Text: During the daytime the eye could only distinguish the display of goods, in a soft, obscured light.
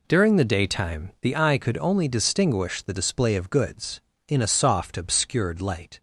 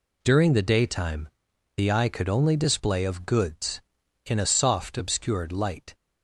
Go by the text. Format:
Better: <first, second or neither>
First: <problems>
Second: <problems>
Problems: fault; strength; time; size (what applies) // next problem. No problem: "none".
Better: first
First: none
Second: pauses between "daytime" and "the"; noticeable; at 1.2 s; 0.48 s long // skips "distinguish the"; at 2.5 s